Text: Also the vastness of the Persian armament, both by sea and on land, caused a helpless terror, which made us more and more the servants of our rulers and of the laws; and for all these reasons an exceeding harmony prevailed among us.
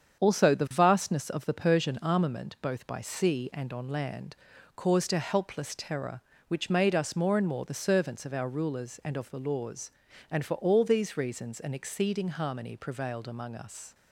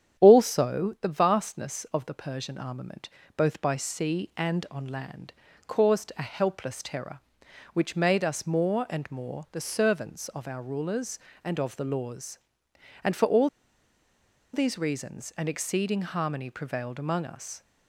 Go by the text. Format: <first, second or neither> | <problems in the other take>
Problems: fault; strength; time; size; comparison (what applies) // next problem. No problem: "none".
first | starts louder than the rest; strong; until 1.2 s; 9.5 dB; strong in the first // pauses between "all" and "these"; at 13.4 s; 1.0 s long